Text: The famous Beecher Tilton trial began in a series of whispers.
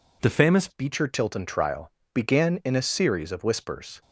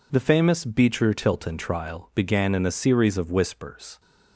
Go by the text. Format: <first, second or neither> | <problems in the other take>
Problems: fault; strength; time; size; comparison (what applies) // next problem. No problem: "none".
second | changes voice at "Beecher"; from 0.6 s on; 3.4 s long // pauses between "trial" and "began"; slight; at 1.9 s; 0.22 s long